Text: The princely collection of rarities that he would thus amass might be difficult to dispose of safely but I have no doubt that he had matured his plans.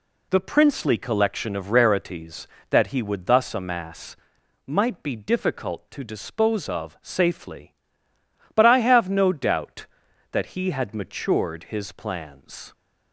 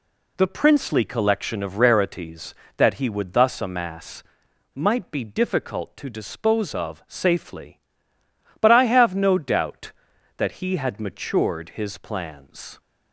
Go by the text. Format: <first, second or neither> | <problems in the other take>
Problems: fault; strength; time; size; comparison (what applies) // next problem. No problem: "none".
neither | pauses between "amass" and "might"; noticeable; the same in both